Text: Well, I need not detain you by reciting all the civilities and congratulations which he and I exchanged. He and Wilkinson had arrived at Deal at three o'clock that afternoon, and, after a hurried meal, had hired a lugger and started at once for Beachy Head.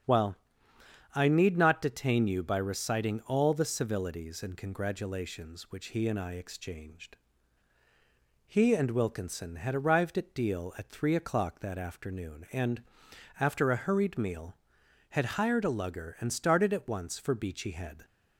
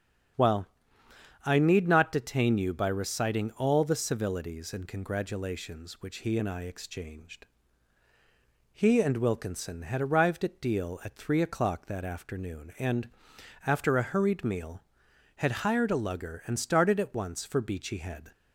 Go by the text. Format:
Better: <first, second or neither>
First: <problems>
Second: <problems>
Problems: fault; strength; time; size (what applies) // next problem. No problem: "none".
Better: neither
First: starts louder than the rest; strong; until 1.8 s; 8 dB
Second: starts louder than the rest; strong; until 2.1 s; 8 dB